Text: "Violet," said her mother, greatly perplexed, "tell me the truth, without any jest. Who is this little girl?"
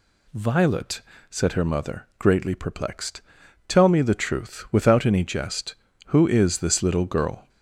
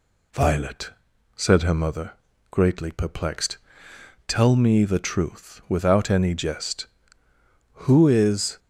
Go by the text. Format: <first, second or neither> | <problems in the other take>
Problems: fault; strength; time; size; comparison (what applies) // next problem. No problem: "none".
first | stops before "this little girl"; at 8.5 s